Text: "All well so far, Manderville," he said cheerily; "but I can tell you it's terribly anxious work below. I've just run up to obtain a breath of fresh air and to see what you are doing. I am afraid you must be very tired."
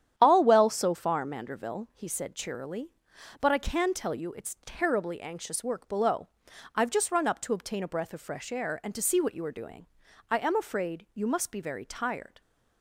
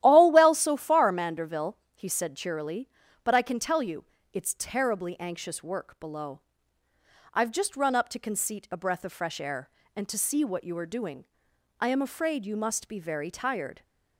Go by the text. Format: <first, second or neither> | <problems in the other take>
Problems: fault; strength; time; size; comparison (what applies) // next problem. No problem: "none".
first | starts louder than the rest; strong; until 1.0 s; 12.5 dB; strong in the first // pauses between "you" and "it's"; slight; at 4.0 s; 0.26 s long // says "conceit" for "obtain"; at 8.1 s